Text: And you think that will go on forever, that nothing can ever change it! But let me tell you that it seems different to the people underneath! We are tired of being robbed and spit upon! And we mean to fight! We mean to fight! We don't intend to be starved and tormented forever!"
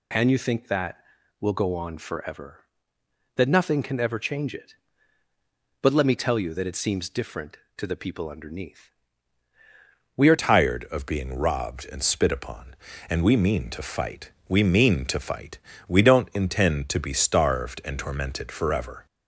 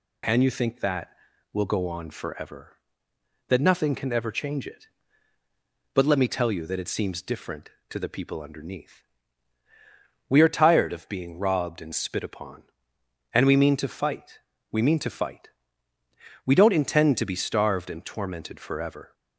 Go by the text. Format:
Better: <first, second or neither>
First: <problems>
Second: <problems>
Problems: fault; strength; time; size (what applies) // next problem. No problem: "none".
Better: second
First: changes voice at "tired"; from 10.3 s on; 8.7 s long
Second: none